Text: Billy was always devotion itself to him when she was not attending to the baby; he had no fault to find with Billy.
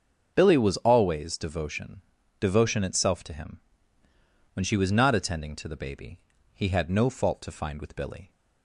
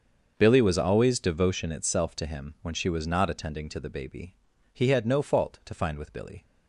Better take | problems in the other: second | starts louder than the rest; until 1.3 s; 6.5 dB; also in the second // says "devotion" twice; at 2.3 s // pauses between "him" and "when"; noticeable; at 3.5 s; 0.94 s long

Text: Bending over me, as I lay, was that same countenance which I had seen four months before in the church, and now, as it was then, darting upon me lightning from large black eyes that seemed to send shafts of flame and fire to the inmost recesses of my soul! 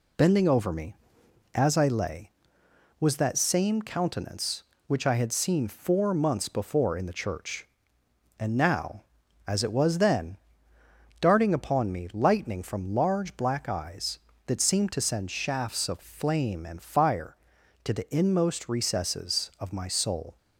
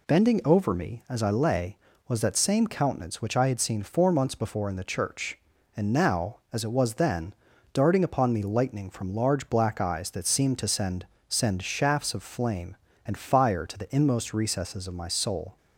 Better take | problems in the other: first | says "send" twice; at 11.2 s

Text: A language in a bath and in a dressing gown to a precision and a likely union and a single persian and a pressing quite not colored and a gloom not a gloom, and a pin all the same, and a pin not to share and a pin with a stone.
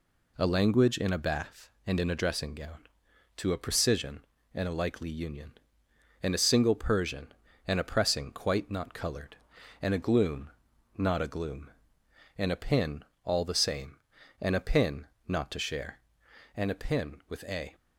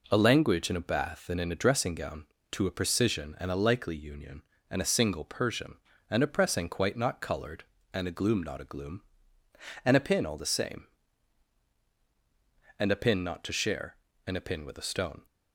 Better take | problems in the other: second | pauses between "gloom" and "not"; noticeable; at 10.4 s; 0.46 s long // pauses between "pin" and "all"; slight; at 13.0 s; 0.20 s long // pauses between "pin" and "not"; slight; at 15.0 s; 0.20 s long // stops before "stone"; at 17.7 s

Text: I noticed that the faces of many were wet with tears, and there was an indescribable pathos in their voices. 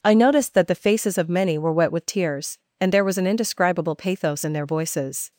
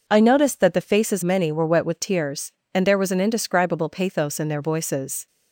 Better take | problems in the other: first | skips "of"; at 1.2 s

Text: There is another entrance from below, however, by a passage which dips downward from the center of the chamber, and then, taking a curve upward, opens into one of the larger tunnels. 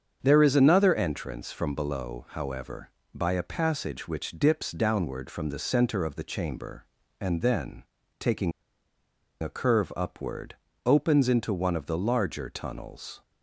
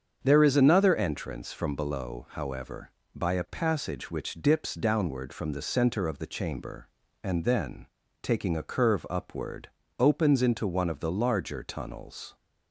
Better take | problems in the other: second | starts louder than the rest; strong; until 1.2 s; 7 dB; strong in the second // pauses between "taking" and "a"; noticeable; at 8.5 s; 0.90 s long

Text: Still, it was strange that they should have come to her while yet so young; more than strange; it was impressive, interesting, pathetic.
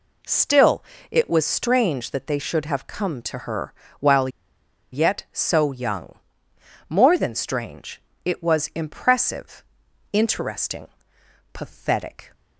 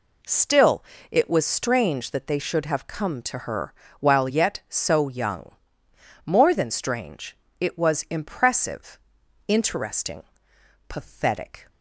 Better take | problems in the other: second | pauses between "her" and "while"; slight; at 3.7 s; 0.28 s long; slight in the second // pauses between "while" and "yet"; noticeable; at 4.2 s; 0.64 s long

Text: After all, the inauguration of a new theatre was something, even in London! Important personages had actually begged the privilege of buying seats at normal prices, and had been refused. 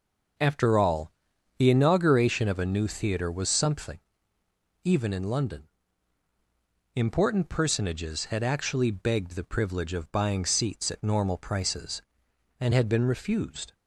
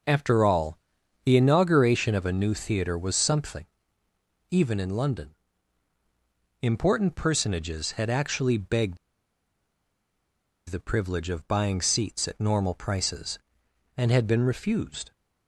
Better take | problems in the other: first | pauses between "begged" and "the"; strong; at 8.9 s; 1.6 s long

